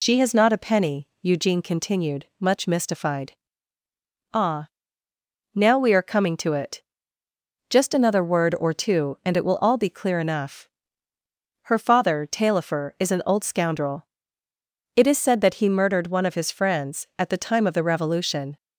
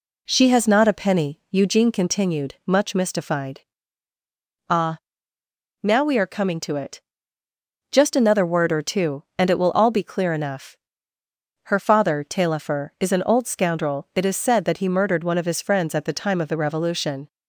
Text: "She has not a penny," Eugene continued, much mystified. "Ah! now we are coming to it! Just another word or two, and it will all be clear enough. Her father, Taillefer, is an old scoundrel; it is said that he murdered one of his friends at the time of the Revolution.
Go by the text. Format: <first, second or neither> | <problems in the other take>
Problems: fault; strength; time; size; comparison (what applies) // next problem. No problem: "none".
second | loses the start of "She"; at 0.0 s; 55 ms